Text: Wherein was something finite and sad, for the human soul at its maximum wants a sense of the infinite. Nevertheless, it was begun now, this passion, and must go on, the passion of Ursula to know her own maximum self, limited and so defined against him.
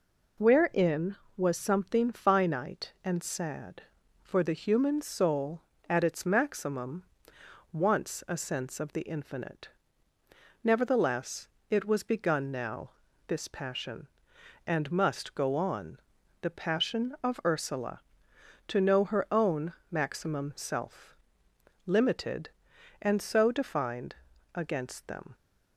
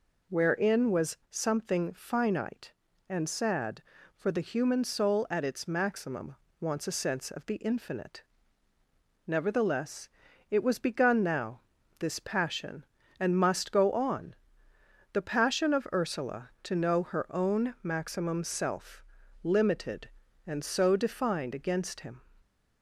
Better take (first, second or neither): second